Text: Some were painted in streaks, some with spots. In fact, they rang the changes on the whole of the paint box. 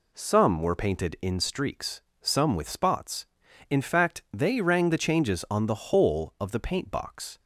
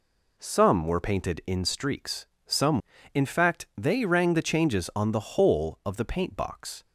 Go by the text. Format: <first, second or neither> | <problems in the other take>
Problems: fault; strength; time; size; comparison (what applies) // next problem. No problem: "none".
first | skips "with spots"; at 2.9 s